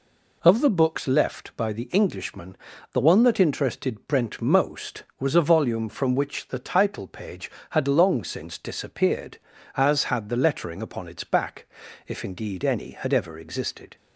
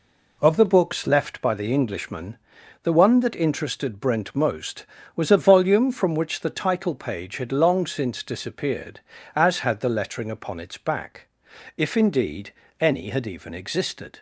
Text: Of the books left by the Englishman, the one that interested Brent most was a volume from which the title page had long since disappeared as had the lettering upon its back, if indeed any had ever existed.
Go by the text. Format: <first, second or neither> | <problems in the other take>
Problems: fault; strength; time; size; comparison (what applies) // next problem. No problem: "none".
first | pauses between "indeed" and "any"; slight; at 12.5 s; 0.26 s long // says "even" for "ever"; at 13.2 s